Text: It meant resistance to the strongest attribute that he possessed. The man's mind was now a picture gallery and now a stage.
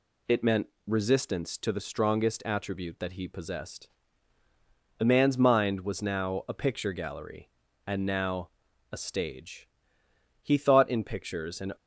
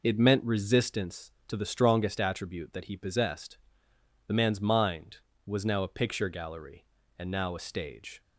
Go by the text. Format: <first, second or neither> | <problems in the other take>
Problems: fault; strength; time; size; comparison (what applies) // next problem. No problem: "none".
second | pauses between "meant" and "resistance"; slight; at 0.6 s; 0.20 s long // pauses between "now" and "a"; at 8.4 s; 0.42 s long // goes on to say "He thought in pictures and"; from 10.4 s on; 1.3 s long